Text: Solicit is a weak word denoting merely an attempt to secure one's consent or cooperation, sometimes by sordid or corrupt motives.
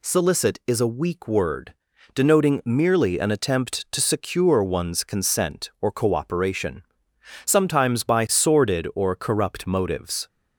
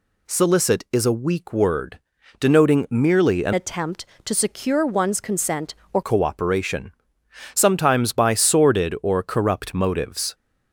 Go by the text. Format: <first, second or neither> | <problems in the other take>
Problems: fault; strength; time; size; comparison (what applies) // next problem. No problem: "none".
first | pauses between "word" and "denoting"; at 1.9 s; 0.42 s long; also in the first // changes voice from "attempt" to "or"; from 3.5 to 6.0 s; 2.5 s long